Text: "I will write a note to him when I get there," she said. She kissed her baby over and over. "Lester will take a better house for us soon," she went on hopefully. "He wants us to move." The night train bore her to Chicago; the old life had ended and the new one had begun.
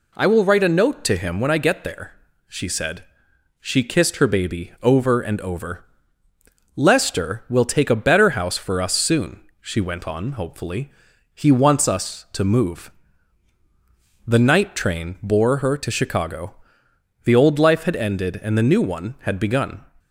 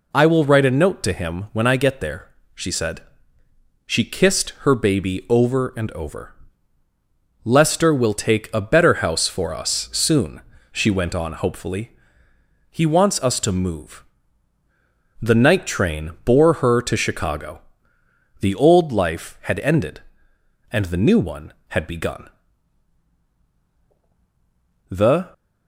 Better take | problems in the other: first | goes on to say "The"; slight; from 24.8 s on; 0.44 s long

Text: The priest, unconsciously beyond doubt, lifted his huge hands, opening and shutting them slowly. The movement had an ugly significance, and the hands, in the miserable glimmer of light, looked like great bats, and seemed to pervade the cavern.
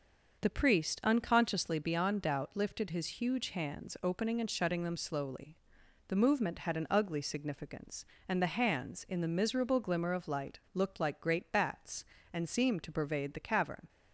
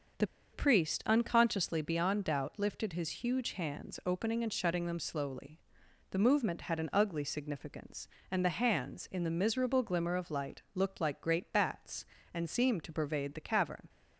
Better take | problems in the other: first | starts louder than the rest; noticeable; until 1.4 s; 6 dB; also in the first // pauses between "The" and "priest"; slight; at 0.2 s; 0.25 s long

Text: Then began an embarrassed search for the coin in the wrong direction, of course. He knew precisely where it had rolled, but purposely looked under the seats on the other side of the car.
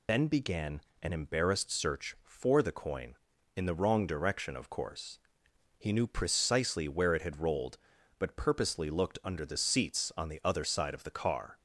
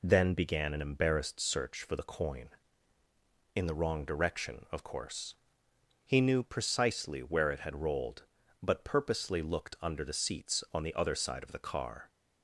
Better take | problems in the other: second | loses the start of "Then"; at 0.0 s; 65 ms // pauses between "began" and "an"; slight; at 0.8 s; 0.22 s long

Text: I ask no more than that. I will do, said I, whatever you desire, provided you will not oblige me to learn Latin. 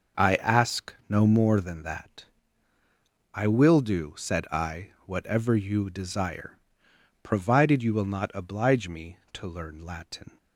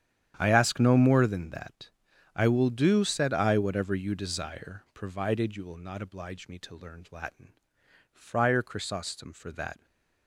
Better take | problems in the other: first | starts louder than the rest; strong; until 1.3 s; 9.5 dB // goes on to say "Friar Chrysostom for that"; strong; from 8.1 s on; 1.7 s long

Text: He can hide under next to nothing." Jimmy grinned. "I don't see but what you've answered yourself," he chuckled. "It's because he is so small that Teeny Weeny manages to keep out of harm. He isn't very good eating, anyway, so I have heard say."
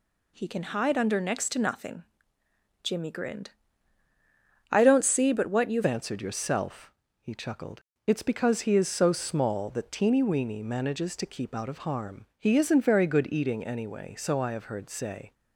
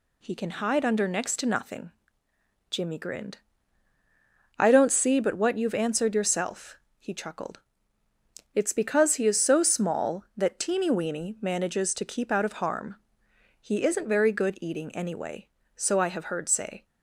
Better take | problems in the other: second | changes voice at "answered"; from 5.8 s on; 9.5 s long

